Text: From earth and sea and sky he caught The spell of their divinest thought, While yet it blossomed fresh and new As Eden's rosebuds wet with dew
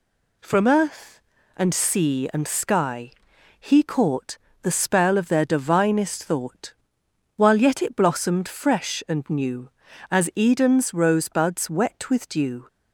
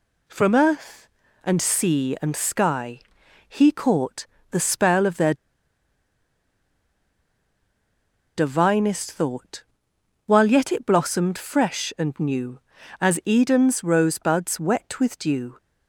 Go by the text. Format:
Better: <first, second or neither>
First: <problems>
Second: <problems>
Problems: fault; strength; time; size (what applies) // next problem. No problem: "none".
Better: first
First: pauses between "sky" and "he"; noticeable; at 3.1 s; 0.48 s long // pauses between "caught" and "The"; slight; at 4.3 s; 0.26 s long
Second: pauses between "sky" and "he"; noticeable; at 2.9 s; 0.48 s long // pauses between "caught" and "The"; slight; at 4.2 s; 0.26 s long // pauses between "their" and "divinest"; strong; at 5.3 s; 3.0 s long